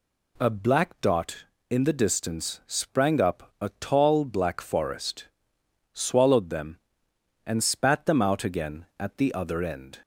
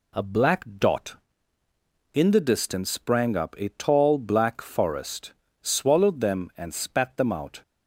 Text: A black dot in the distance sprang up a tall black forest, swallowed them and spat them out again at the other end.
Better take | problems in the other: first | stops before "again at the other end"; at 7.6 s

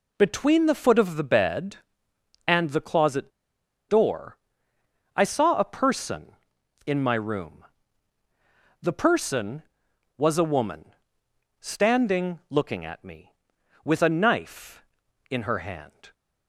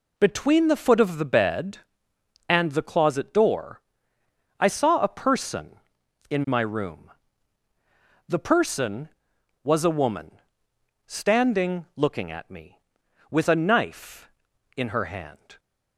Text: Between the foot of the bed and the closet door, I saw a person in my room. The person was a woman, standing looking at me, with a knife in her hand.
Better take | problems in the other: second | pauses between "closet" and "door"; noticeable; at 3.3 s; 0.59 s long

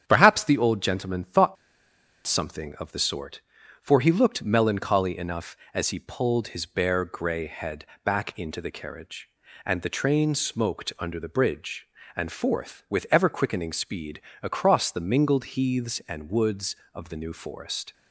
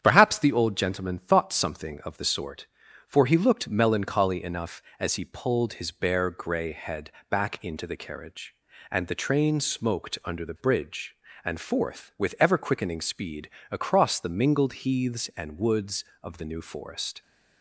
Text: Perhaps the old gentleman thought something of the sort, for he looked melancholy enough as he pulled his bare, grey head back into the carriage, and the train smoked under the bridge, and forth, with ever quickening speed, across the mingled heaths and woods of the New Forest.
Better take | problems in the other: second | starts louder than the rest; strong; until 1.0 s; 8.5 dB; strong in the second // pauses between "thought" and "something"; noticeable; at 1.5 s; 0.71 s long // pauses between "head" and "back"; slight; at 7.8 s; 0.20 s long; slight in the second

